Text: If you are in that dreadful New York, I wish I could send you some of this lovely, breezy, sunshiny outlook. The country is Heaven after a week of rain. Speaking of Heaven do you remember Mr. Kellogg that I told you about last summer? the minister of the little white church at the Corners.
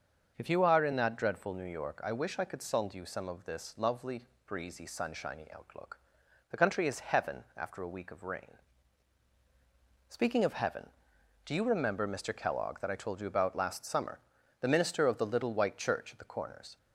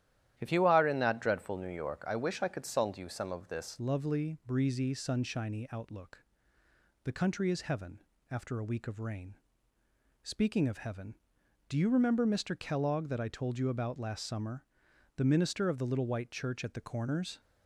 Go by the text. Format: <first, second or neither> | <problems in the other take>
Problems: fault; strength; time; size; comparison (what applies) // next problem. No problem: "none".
first | starts louder than the rest; strong; until 1.3 s; 12 dB; also in the first // changes voice at "lovely"; from 3.7 s on; 13.6 s long // pauses between "Heaven" and "after"; slight; at 7.9 s; 0.30 s long